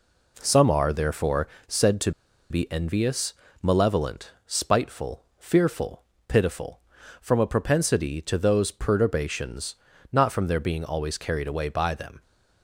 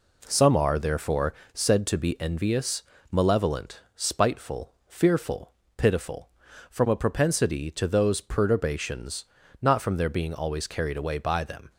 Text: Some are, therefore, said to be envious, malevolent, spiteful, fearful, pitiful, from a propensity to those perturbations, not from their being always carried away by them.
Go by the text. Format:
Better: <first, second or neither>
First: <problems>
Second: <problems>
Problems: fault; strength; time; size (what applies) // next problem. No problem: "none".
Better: second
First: pauses between "to" and "be"; at 2.1 s; 0.38 s long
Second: none